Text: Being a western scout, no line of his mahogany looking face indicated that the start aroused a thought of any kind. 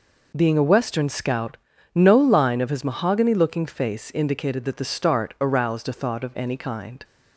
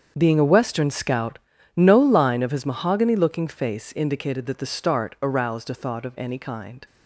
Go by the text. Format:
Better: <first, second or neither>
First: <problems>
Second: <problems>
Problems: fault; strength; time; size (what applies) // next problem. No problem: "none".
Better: first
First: none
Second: gets quieter; strong; throughout; 14.5 dB